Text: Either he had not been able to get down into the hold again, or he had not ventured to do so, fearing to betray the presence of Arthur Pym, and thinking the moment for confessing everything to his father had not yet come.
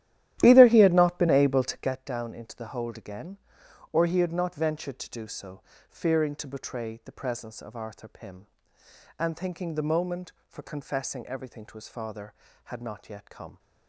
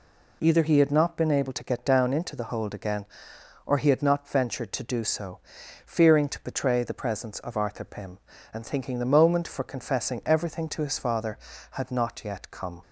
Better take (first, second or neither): second